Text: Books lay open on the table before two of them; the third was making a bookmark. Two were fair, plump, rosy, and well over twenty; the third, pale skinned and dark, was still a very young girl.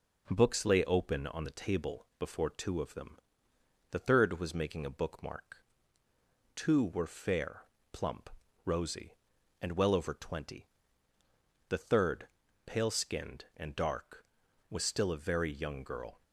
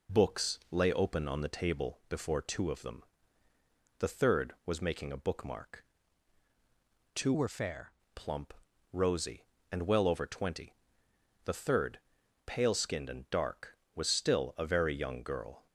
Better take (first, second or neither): first